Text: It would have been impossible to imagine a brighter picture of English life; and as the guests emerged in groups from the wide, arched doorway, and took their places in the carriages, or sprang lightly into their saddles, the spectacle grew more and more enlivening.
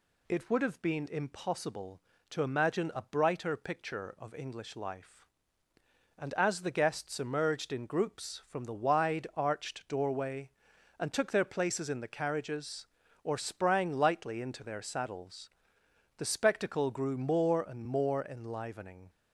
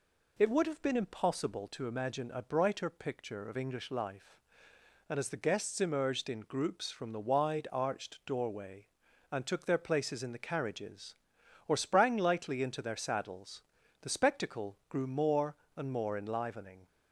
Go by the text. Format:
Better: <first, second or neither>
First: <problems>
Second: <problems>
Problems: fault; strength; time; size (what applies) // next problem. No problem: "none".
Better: neither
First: none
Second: none